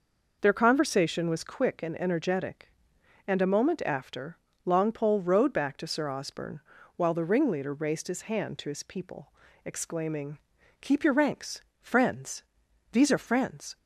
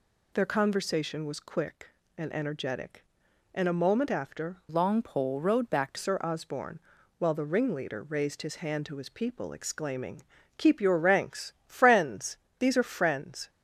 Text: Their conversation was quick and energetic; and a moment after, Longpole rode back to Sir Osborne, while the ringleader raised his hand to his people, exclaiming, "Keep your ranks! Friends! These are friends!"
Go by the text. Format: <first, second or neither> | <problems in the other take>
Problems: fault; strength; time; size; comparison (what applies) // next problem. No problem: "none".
first | changes voice from "Longpole" to "to"; from 4.6 to 5.9 s; 1.3 s long